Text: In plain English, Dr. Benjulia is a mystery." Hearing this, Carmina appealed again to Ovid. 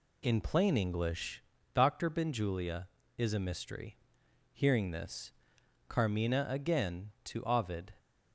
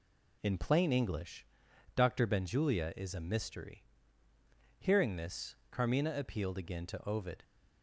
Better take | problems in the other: second | skips "appealed"; at 6.4 s

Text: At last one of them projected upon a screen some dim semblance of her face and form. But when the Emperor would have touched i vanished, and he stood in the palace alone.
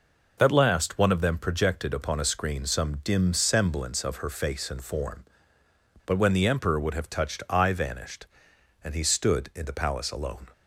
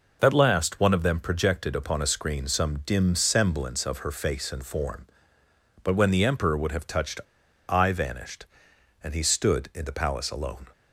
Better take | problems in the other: first | pauses between "touched" and "i"; noticeable; at 7.2 s; 0.46 s long

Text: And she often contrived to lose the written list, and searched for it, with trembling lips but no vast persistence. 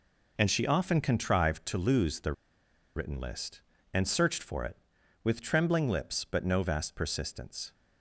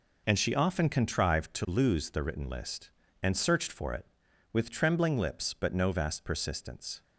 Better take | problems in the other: second | pauses between "the" and "written"; noticeable; at 2.3 s; 0.63 s long

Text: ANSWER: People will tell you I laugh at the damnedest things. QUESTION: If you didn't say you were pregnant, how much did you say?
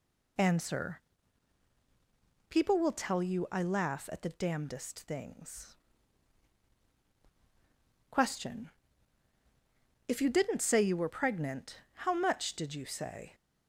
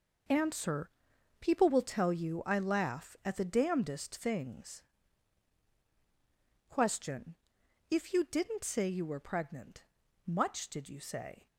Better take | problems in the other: first | skips "how"; at 10.0 s

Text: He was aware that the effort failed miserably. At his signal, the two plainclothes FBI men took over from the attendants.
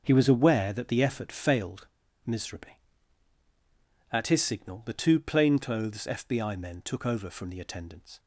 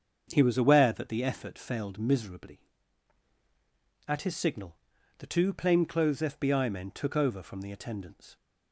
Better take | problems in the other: second | starts louder than the rest; until 1.0 s; 6 dB; also in the second // pauses between "failed" and "miserably"; at 1.8 s; 0.38 s long

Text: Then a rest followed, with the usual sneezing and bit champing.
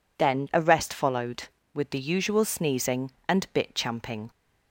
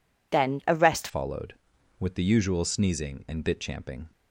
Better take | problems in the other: first | changes voice at "followed"; from 1.0 s on; 3.0 s long

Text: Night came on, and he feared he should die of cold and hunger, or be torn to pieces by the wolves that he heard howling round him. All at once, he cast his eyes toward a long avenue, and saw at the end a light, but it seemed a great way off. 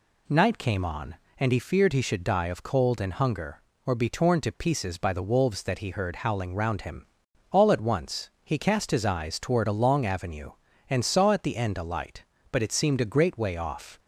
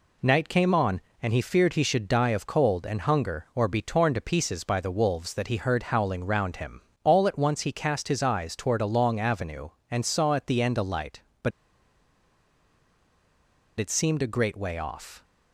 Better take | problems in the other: first | pauses between "but" and "it"; strong; at 11.5 s; 2.2 s long

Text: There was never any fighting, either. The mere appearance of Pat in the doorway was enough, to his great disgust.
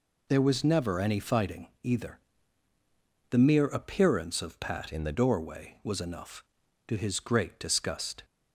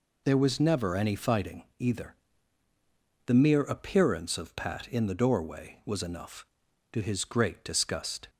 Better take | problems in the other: second | changes voice from "in" to "the"; from 4.9 to 5.1 s; 0.2 s long

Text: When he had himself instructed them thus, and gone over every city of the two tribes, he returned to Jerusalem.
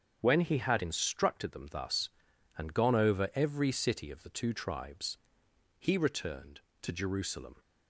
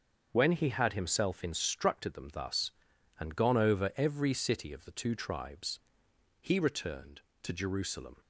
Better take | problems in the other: second | starts louder than the rest; until 1.2 s; 7 dB; also in the second // skips "himself"; at 0.8 s

